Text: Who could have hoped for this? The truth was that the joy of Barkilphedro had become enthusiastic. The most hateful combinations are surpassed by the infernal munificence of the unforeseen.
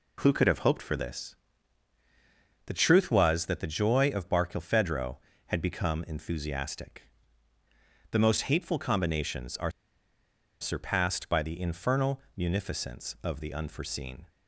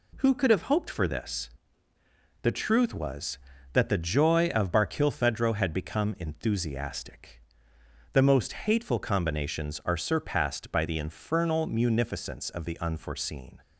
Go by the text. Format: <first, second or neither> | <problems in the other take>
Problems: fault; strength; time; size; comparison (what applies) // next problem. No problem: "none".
second | pauses between "are" and "surpassed"; noticeable; at 9.7 s; 0.89 s long // pauses between "infernal" and "munificence"; slight; at 12.2 s; 0.16 s long